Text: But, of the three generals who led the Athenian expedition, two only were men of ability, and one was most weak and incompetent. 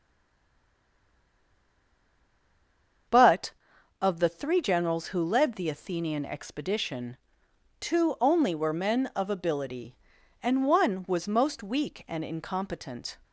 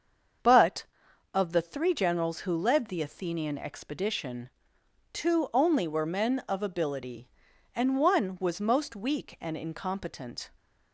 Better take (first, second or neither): second